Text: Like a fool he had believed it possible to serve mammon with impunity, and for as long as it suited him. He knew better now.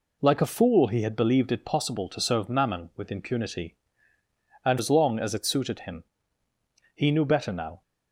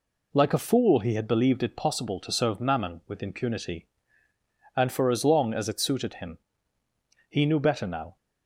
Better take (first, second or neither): second